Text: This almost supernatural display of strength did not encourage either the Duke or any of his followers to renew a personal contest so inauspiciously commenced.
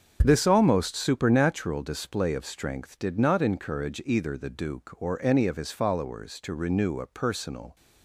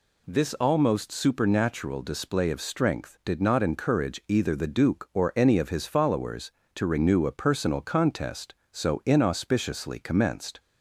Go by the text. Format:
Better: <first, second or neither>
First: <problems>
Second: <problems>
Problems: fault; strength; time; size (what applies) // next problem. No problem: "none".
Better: second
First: starts louder than the rest; until 1.2 s; 6.5 dB // stops before "contest so inauspiciously commenced"; at 7.7 s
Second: none